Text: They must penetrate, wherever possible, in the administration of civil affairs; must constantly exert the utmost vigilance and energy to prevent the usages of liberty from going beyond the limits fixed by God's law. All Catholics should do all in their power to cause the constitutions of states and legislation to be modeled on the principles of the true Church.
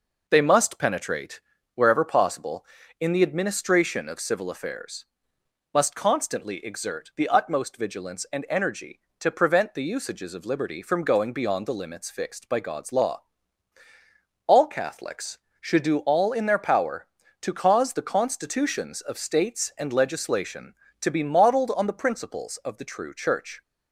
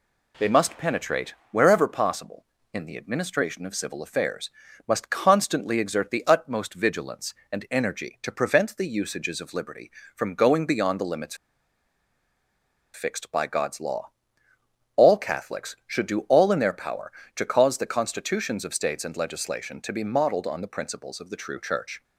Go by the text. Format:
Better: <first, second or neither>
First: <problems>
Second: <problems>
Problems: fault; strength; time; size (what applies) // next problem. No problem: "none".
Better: first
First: none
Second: pauses between "limits" and "fixed"; strong; at 11.3 s; 1.5 s long